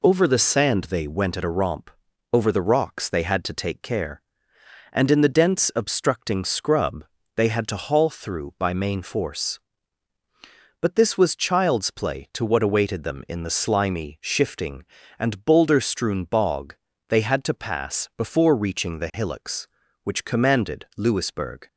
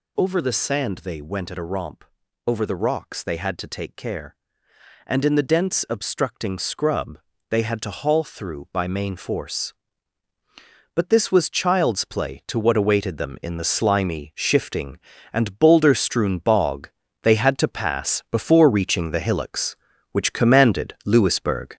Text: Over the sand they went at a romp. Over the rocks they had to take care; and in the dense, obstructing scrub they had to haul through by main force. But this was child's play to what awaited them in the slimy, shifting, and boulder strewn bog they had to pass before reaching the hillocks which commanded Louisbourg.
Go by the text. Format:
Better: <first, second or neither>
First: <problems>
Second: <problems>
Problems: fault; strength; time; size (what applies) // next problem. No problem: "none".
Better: first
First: pauses between "scrub" and "they"; slight; at 7.0 s; 0.32 s long // pauses between "bog" and "they"; slight; at 16.7 s; 0.36 s long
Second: gets louder; noticeable; throughout; 5.5 dB // pauses between "scrub" and "they"; slight; at 7.1 s; 0.32 s long // pauses between "bog" and "they"; slight; at 16.8 s; 0.36 s long